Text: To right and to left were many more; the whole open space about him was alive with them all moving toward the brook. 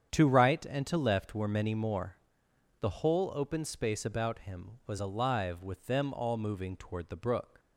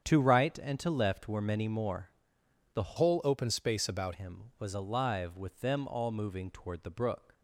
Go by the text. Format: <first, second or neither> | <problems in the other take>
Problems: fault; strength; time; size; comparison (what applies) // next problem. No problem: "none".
first | starts louder than the rest; strong; until 1.0 s; 8 dB; strong in the first // changes voice from "whole" to "about"; from 2.9 to 4.1 s; 1.2 s long